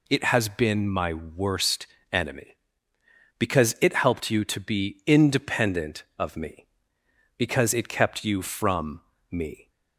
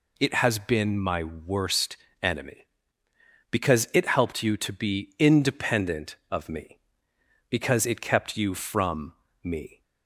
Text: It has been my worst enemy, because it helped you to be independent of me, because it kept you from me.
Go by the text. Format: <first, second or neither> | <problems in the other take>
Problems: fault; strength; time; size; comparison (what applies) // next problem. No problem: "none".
neither | pauses between "worst" and "enemy"; slight; the same in both // pauses between "from" and "me"; slight; the same in both